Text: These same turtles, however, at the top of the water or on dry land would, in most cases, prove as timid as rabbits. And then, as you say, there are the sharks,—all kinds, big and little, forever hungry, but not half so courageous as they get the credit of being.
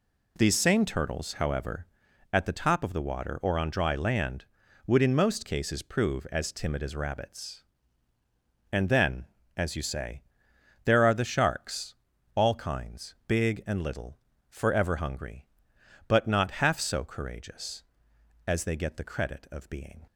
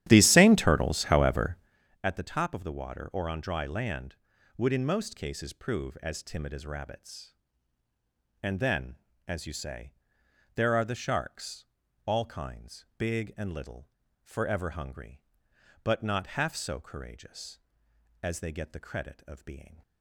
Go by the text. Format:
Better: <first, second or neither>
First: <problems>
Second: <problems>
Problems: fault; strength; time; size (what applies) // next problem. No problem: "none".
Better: first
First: none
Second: starts louder than the rest; strong; until 1.9 s; 12 dB